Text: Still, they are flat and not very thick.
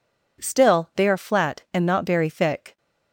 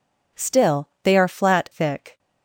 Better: first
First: none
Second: skips "and not very"; at 1.7 s

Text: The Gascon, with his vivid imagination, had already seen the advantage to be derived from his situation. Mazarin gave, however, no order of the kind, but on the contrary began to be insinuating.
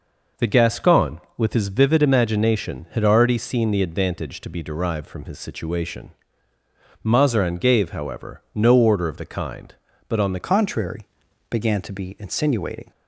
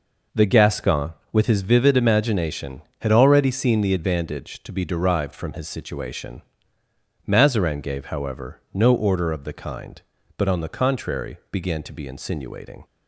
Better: second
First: changes voice at "contrary"; from 10.4 s on; 2.5 s long // pauses between "contrary" and "began"; at 11.0 s; 0.42 s long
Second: none

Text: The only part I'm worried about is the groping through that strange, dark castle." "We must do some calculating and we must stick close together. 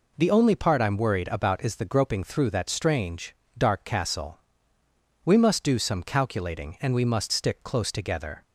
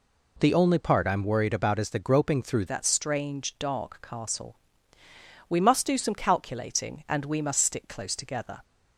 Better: first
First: none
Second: changes voice at "that"; from 2.6 s on; 6.0 s long

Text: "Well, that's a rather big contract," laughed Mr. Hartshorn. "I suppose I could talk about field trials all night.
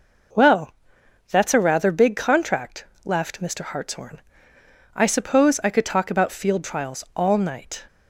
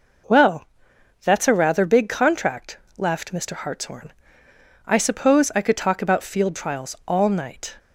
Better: neither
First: none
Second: none

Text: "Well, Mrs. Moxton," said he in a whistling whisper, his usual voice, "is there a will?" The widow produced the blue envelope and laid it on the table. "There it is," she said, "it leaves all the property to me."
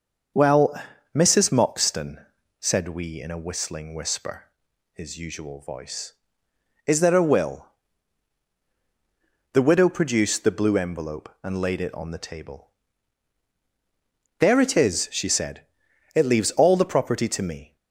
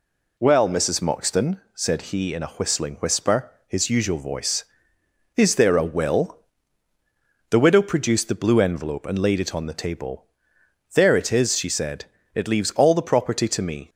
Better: second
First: starts louder than the rest; until 1.7 s; 6.5 dB // says "we" for "he"; at 2.8 s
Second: none

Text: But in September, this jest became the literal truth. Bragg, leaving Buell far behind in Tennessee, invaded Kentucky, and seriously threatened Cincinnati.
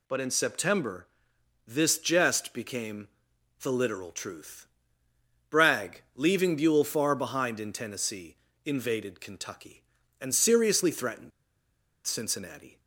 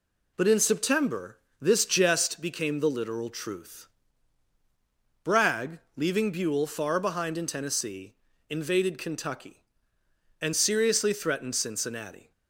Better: second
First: pauses between "became" and "the"; noticeable; at 3.0 s; 0.54 s long // pauses between "threatened" and "Cincinnati"; noticeable; at 11.3 s; 0.76 s long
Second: none

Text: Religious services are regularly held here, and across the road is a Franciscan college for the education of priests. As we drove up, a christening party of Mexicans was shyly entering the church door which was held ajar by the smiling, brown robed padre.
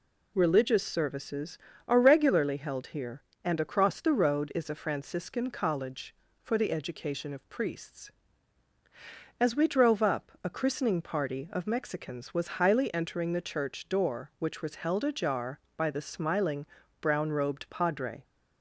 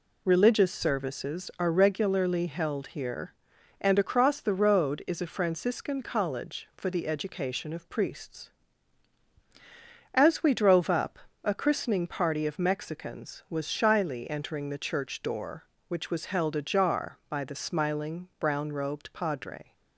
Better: second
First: says "highly" for "shyly"; at 12.5 s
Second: none

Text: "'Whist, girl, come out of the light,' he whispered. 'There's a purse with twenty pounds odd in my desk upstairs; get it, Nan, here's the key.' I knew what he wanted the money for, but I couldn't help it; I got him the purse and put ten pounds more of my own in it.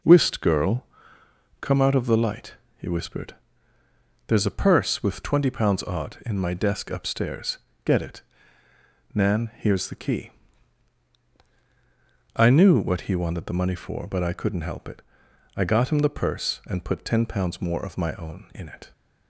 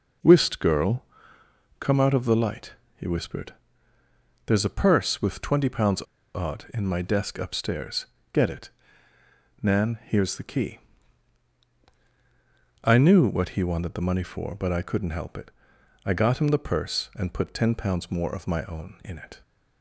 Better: first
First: none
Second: pauses between "pounds" and "odd"; slight; at 6.0 s; 0.32 s long

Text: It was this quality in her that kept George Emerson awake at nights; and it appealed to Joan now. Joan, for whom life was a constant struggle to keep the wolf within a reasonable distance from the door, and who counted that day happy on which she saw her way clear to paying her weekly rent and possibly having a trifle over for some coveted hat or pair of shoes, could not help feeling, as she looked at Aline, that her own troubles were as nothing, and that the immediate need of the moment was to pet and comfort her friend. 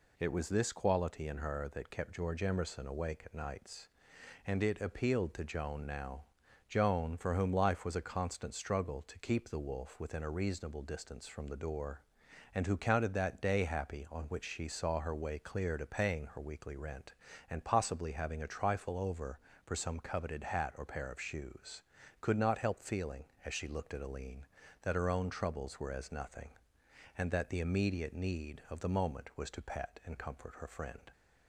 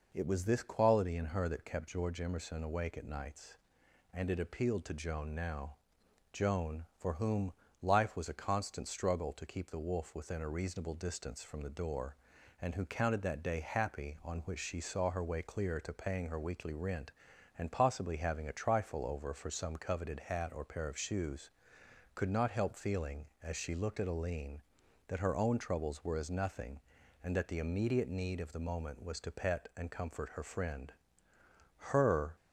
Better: first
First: none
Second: pauses between "whom" and "life"; slight; at 7.5 s; 0.28 s long // goes on to say "Her"; from 31.7 s on; 0.58 s long

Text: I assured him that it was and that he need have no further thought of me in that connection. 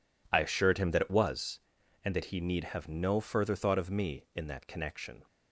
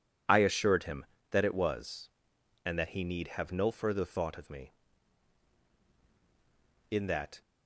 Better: first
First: none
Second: stops before "connection"; at 7.4 s

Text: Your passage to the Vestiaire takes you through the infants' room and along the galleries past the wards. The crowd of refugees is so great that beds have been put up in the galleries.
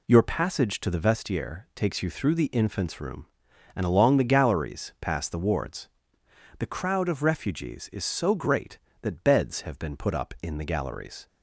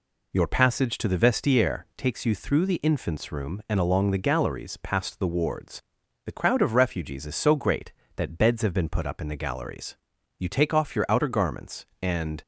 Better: first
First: none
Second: goes on to say "You take off your outer garments and"; strong; from 10.3 s on; 2.0 s long

